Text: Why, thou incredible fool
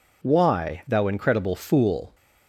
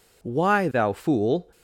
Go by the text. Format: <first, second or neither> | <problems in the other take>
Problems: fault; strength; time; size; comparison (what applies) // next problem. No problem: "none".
first | skips "incredible"; at 0.9 s